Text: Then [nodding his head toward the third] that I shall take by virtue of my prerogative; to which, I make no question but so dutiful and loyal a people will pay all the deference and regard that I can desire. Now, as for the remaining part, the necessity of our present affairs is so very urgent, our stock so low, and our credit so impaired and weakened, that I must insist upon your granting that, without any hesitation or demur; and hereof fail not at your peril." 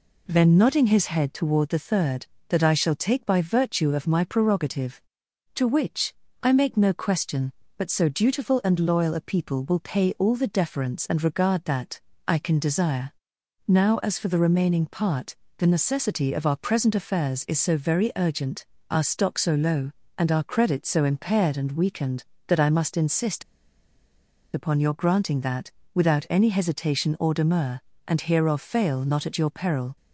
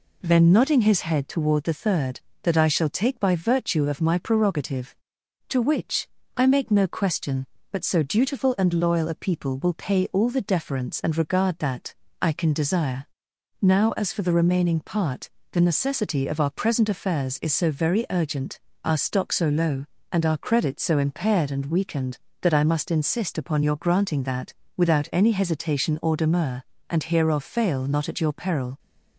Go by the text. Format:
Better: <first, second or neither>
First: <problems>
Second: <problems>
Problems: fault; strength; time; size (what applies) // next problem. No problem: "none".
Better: second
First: pauses between "that" and "I"; slight; at 12.0 s; 0.26 s long // pauses between "insist" and "upon"; at 23.4 s; 1.1 s long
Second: pauses between "that" and "I"; slight; at 11.9 s; 0.26 s long